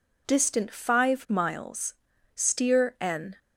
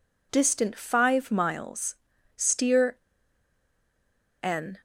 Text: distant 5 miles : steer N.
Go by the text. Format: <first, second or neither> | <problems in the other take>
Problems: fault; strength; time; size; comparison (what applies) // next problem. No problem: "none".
first | pauses between "steer" and "N"; strong; at 2.9 s; 1.4 s long